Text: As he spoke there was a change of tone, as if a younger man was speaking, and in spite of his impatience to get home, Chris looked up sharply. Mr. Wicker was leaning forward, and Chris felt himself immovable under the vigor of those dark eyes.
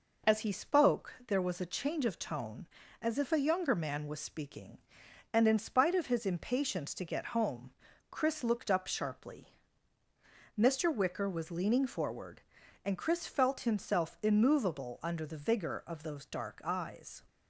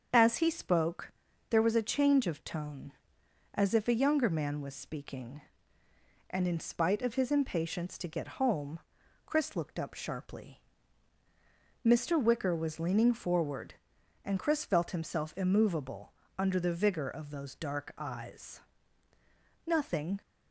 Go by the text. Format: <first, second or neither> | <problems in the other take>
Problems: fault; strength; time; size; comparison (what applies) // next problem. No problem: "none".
first | starts louder than the rest; until 1.5 s; 7 dB // pauses between "spoke" and "there"; at 1.1 s; 0.40 s long // pauses between "immovable" and "under"; slight; at 16.1 s; 0.28 s long // goes on to say "Nothing"; from 19.6 s on; 0.54 s long